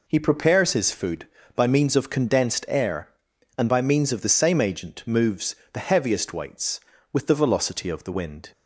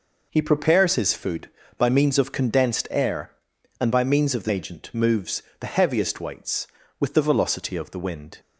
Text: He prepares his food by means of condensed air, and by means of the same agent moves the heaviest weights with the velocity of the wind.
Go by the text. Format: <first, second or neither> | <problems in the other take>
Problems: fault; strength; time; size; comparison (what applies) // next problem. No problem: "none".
first | skips "same"; at 4.4 s // pauses between "moves" and "the"; slight; at 5.4 s; 0.20 s long; slight in the first